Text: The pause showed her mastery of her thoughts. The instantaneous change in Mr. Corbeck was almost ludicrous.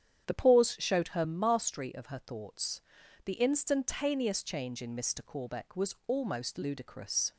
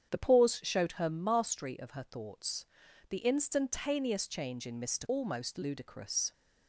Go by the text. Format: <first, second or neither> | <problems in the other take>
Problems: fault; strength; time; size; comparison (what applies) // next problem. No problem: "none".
first | starts louder than the rest; strong; until 1.1 s; 8.5 dB; strong in the first // skips "Corbeck was"; at 5.0 s